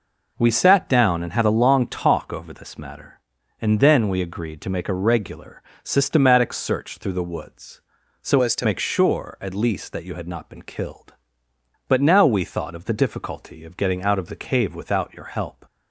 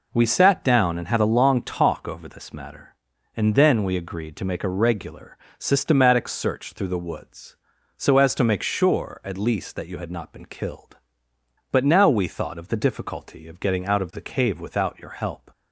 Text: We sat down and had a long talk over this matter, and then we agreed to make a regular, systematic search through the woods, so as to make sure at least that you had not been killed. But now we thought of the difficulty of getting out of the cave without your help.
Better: second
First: changes voice from "as" to "to"; from 8.4 to 8.6 s; 0.2 s long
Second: none

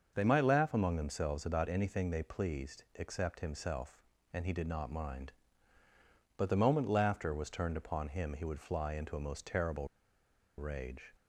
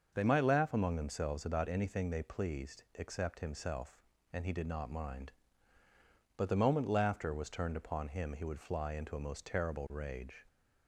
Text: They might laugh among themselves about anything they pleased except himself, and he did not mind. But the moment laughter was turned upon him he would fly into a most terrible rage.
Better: second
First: starts louder than the rest; until 1.1 s; 6.5 dB // pauses between "terrible" and "rage"; noticeable; at 9.8 s; 0.71 s long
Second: starts louder than the rest; until 1.1 s; 6.5 dB

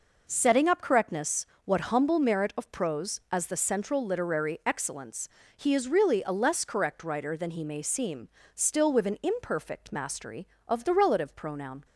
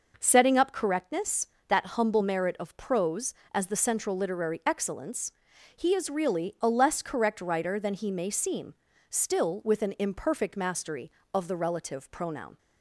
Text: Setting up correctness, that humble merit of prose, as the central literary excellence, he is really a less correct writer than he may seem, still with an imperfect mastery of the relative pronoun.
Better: second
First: says "what" for "that"; at 1.6 s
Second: none

